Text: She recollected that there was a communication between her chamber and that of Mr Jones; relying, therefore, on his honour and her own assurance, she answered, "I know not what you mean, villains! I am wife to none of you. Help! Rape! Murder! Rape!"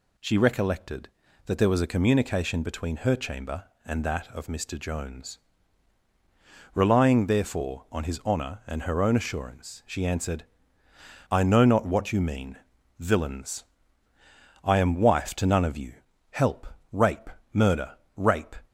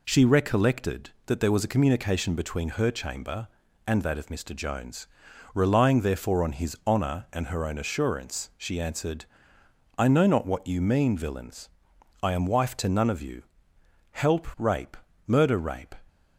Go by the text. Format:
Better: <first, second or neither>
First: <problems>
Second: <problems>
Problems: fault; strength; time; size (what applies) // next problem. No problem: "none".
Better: neither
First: none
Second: none